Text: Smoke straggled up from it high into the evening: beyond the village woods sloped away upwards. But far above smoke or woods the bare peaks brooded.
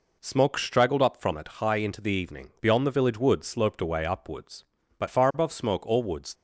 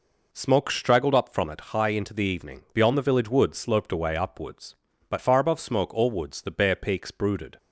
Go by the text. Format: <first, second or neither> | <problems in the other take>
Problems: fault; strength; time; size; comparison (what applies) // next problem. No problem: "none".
second | stops before "the bare peaks brooded"; at 6.3 s